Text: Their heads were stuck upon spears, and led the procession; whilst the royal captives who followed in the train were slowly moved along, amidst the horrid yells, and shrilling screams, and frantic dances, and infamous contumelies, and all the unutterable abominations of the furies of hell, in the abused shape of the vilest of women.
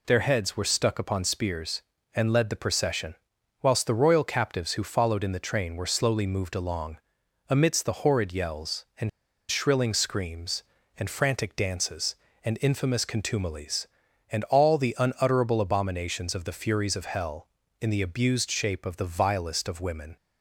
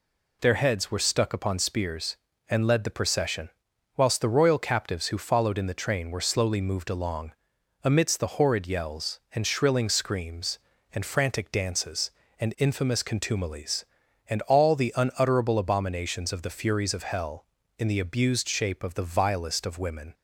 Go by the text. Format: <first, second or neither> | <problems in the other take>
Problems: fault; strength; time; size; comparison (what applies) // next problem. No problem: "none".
second | pauses between "and" and "shrilling"; at 9.0 s; 0.41 s long